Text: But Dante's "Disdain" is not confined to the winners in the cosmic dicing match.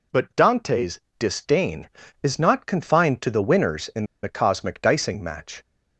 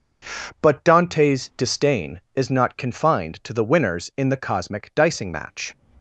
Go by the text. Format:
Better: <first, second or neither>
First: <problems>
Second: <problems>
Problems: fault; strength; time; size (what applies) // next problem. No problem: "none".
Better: second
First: pauses between "Dante's" and "Disdain"; slight; at 0.9 s; 0.20 s long // pauses between "in" and "the"; slight; at 4.0 s; 0.17 s long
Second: none